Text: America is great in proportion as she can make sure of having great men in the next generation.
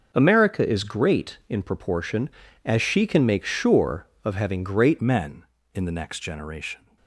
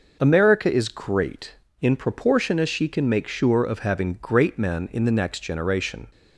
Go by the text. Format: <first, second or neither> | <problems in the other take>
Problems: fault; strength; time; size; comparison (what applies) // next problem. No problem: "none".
second | starts louder than the rest; until 1.1 s; 6 dB // changes voice at "men"; from 5.0 s on; 1.9 s long